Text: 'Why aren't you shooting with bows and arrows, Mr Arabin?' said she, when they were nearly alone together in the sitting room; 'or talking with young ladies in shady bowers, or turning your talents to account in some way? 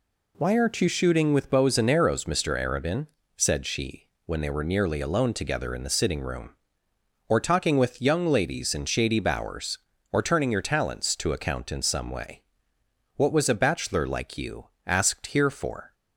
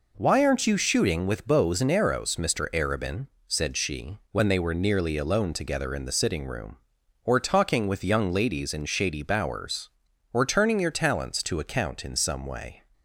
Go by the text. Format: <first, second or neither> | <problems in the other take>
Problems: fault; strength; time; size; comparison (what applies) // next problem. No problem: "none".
second | goes on to say "What was a bachelor like you asked here for"; strong; from 13.1 s on; 2.7 s long